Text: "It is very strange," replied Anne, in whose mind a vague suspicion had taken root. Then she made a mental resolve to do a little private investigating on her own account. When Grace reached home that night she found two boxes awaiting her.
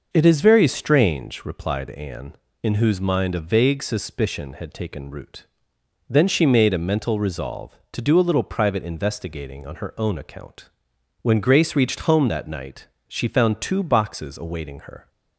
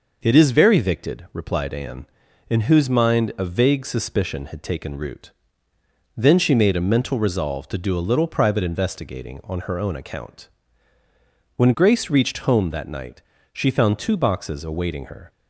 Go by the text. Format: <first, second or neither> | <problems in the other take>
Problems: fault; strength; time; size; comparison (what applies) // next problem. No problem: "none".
first | says "victed" for "strange"; at 0.8 s // pauses between "night" and "she"; slight; at 13.2 s; 0.30 s long; slight in the first